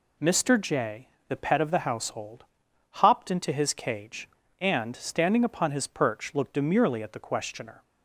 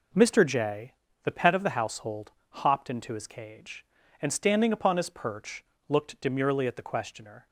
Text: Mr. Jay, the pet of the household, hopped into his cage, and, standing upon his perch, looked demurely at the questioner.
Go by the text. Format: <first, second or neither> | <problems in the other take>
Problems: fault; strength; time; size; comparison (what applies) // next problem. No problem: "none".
neither | none